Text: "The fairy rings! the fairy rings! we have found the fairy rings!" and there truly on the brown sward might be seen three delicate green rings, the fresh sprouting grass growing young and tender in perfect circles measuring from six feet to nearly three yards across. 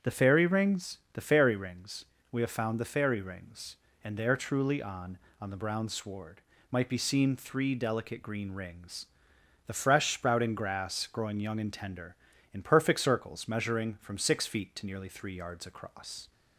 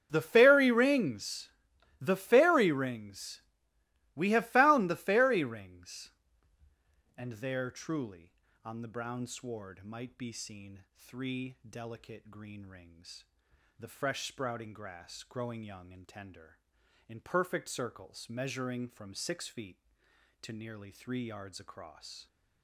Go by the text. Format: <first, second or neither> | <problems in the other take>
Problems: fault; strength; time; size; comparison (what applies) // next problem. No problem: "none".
second | starts louder than the rest; strong; until 1.1 s; 8 dB; strong in the second // says "on" twice; at 5.4 s // pauses between "sward" and "might"; slight; at 6.4 s; 0.30 s long